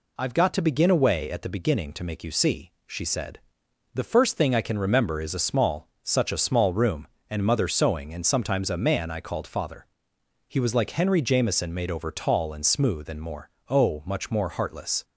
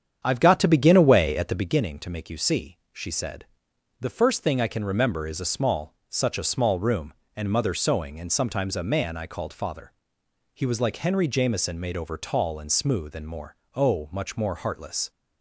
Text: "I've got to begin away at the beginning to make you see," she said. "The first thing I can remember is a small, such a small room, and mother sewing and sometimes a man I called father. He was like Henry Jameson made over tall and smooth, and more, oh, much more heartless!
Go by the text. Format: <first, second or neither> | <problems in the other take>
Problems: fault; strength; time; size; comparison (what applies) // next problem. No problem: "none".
first | starts louder than the rest; strong; until 1.9 s; 8.5 dB